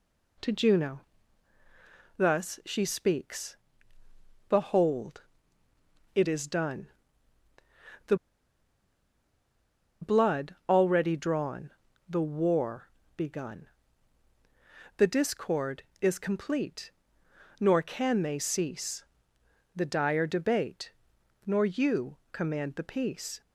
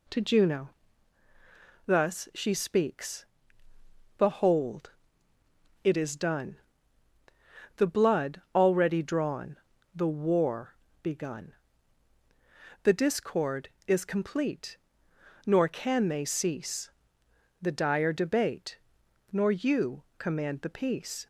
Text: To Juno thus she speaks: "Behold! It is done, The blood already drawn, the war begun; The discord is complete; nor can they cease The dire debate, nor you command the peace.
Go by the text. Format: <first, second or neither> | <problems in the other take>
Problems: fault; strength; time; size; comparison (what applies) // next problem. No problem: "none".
second | pauses between "Juno" and "thus"; at 1.0 s; 1.1 s long; also in the second // pauses between "The" and "blood"; strong; at 8.1 s; 1.8 s long // pauses between "war" and "begun"; slight; at 12.8 s; 0.28 s long; slight in the second // pauses between "cease" and "The"; noticeable; at 19.0 s; 0.72 s long; noticeable in the second